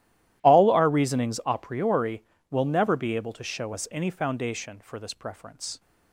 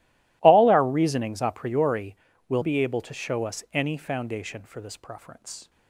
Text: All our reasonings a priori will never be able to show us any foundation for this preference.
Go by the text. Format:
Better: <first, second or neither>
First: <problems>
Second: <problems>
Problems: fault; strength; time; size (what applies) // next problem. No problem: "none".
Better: first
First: none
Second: skips "never"; at 2.6 s